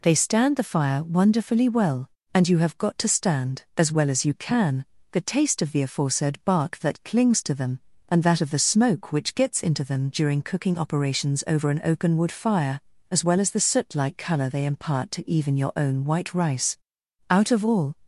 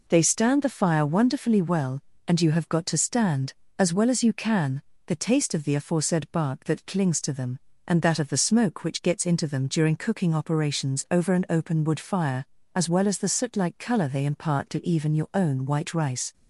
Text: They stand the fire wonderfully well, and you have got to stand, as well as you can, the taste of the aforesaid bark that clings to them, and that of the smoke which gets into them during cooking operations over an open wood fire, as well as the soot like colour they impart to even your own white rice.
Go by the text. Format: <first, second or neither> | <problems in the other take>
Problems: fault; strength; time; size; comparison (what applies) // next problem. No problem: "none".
second | goes on to say "Out of all"; noticeable; from 17.2 s on; 0.70 s long